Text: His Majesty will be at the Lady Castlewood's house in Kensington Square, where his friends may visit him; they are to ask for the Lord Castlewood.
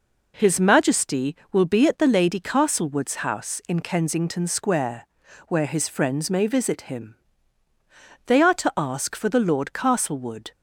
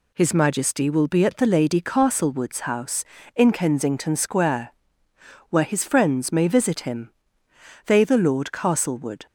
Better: first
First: none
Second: skips "are to ask for"; at 8.0 s

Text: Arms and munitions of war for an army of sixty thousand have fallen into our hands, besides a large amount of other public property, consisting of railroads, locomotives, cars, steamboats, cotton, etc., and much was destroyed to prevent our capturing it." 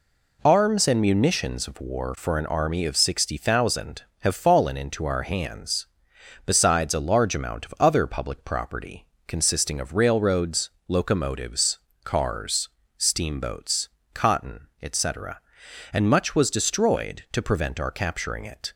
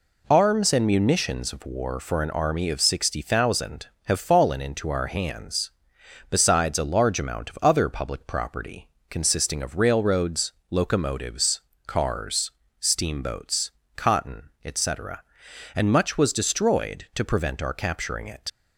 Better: first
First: none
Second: leaves "it" unfinished; at 18.4 s; 55 ms

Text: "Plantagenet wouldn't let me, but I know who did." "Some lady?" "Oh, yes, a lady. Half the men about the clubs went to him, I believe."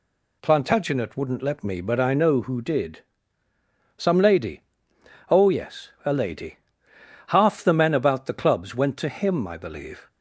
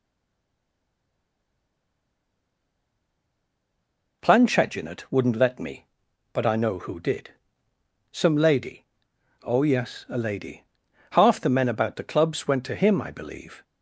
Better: first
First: none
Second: stays silent before the first word; strong; until 4.2 s; 4.2 s long

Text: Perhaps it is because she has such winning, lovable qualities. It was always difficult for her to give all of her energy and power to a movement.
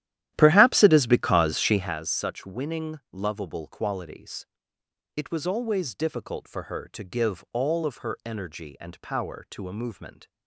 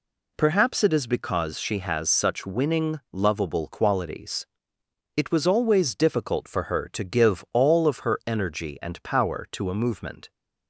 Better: second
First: starts louder than the rest; strong; until 2.0 s; 12.5 dB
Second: none

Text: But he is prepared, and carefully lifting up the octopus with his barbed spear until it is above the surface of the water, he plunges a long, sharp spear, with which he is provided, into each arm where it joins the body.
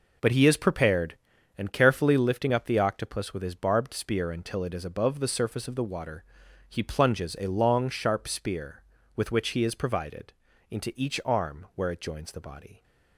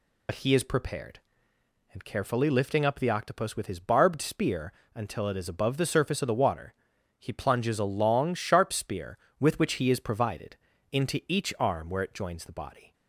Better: first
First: none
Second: loses the start of "But"; at 0.2 s; 55 ms // pauses between "spear" and "until"; slight; at 4.7 s; 0.22 s long

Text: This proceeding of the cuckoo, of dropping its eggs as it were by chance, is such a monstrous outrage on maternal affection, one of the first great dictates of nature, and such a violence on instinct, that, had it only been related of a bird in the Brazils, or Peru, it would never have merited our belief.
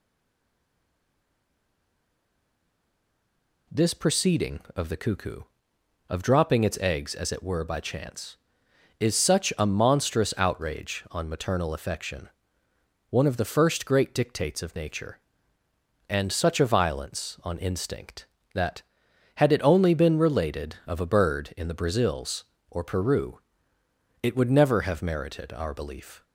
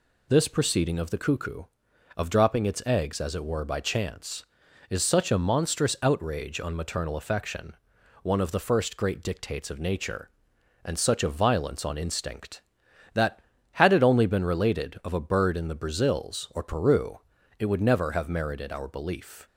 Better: second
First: stays silent before the first word; strong; until 3.6 s; 3.6 s long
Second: none

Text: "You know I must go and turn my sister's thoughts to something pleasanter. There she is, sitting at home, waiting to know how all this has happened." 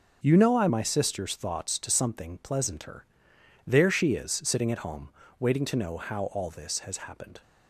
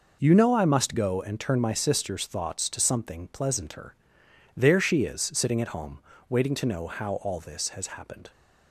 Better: second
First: starts louder than the rest; noticeable; until 1.2 s; 6 dB // skips "must go and turn"; at 0.6 s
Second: none

